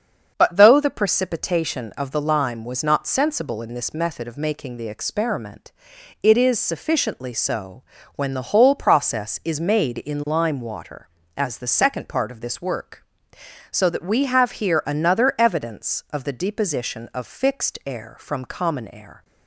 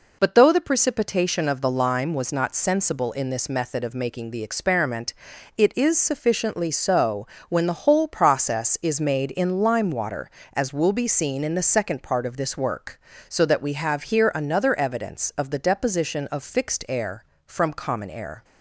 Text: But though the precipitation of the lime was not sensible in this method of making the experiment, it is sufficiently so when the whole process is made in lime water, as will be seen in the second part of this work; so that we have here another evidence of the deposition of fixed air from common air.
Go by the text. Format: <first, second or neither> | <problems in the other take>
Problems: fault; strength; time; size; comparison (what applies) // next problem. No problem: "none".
second | starts louder than the rest; until 1.3 s; 6.5 dB // pauses between "so" and "when"; slight; at 7.8 s; 0.32 s long; slight in the second // skips "will be seen in"; at 11.5 s